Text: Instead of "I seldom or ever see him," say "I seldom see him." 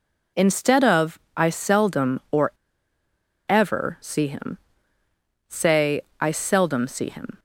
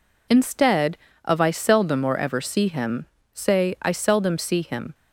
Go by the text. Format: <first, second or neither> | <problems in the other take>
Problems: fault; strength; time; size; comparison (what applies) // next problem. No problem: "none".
second | pauses between "of" and "I"; slight; at 1.1 s; 0.16 s long // pauses between "or" and "ever"; at 2.4 s; 0.99 s long // pauses between "say" and "I"; slight; at 6.0 s; 0.18 s long